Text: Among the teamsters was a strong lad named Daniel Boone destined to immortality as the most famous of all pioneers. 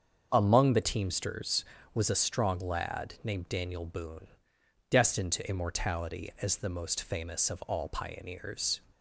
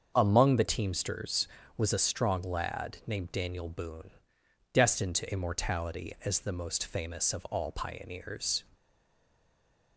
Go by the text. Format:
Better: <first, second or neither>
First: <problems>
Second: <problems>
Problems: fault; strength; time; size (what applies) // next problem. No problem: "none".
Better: first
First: starts louder than the rest; until 1.3 s; 7 dB // pauses between "Boone" and "destined"; noticeable; at 4.2 s; 0.64 s long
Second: starts louder than the rest; until 1.1 s; 7 dB // pauses between "Boone" and "destined"; noticeable; at 4.1 s; 0.64 s long // stays silent after the last word; noticeable; from 8.7 s on; 1.2 s long